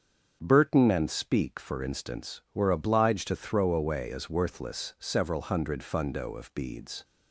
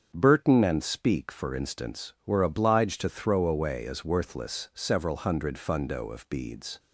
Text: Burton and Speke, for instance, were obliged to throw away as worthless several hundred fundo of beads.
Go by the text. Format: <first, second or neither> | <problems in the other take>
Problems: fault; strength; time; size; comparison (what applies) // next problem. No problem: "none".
neither | starts louder than the rest; the same in both